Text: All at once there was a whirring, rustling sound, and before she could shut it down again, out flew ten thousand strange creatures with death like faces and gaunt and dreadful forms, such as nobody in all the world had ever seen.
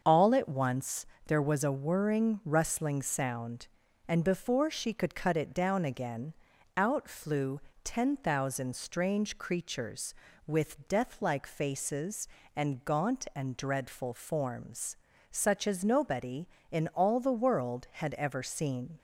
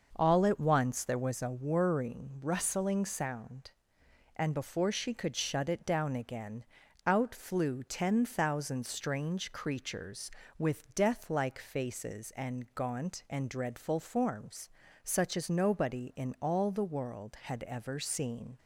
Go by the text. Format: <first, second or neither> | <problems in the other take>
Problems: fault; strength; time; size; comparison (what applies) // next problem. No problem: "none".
second | starts louder than the rest; until 1.0 s; 6.5 dB; noticeable in the second // pauses between "once" and "there"; slight; at 1.0 s; 0.22 s long // says "cut" for "shut"; at 5.1 s // pauses between "flew" and "ten"; slight; at 7.6 s; 0.24 s long